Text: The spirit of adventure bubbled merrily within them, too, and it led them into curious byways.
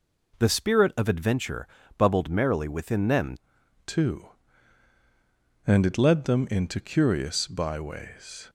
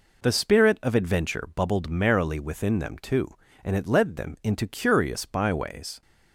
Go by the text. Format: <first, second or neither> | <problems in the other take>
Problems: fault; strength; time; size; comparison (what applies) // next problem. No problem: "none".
second | pauses between "adventure" and "bubbled"; slight; at 1.6 s; 0.30 s long // changes voice at "too"; from 3.8 s on; 4.6 s long